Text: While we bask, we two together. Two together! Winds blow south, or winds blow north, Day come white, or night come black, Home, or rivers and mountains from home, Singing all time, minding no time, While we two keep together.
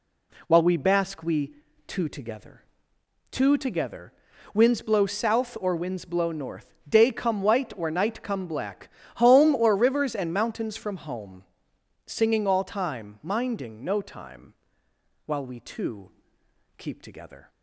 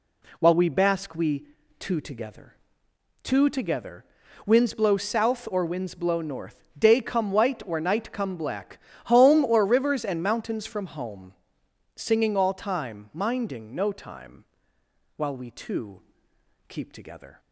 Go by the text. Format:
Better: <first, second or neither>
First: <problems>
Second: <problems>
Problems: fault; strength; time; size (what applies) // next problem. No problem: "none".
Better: neither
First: pauses between "we" and "two"; slight; at 1.5 s; 0.32 s long // pauses between "two" and "keep"; noticeable; at 16.1 s; 0.66 s long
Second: pauses between "we" and "two"; slight; at 1.4 s; 0.32 s long // pauses between "two" and "keep"; noticeable; at 16.0 s; 0.66 s long